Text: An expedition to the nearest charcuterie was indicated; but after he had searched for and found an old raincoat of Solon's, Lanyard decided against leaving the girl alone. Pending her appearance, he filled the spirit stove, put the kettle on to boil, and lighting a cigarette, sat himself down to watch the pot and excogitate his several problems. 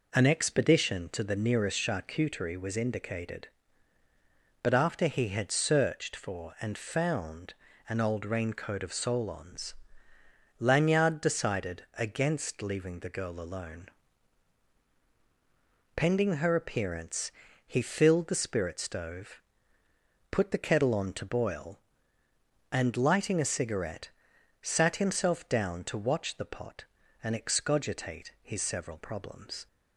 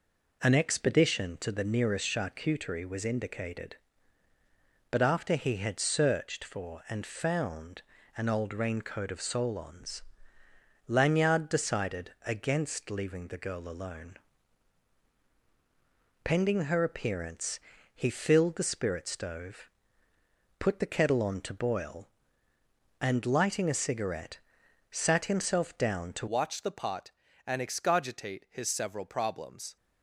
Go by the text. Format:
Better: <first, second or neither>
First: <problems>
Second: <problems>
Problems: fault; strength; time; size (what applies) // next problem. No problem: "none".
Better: first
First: pauses between "found" and "an"; at 7.5 s; 0.38 s long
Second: pauses between "found" and "an"; at 7.7 s; 0.38 s long // changes voice at "watch"; from 26.2 s on; 3.5 s long